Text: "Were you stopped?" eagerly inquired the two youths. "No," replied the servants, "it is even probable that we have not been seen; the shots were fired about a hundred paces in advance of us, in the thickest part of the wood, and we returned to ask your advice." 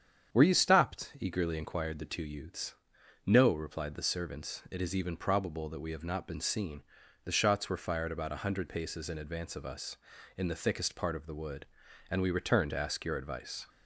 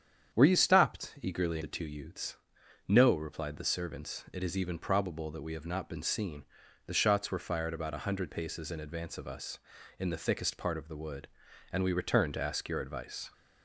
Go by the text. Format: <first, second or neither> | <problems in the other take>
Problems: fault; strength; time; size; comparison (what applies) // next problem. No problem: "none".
first | starts louder than the rest; strong; until 1.4 s; 8.5 dB; strong in the first // skips "inquired"; at 1.6 s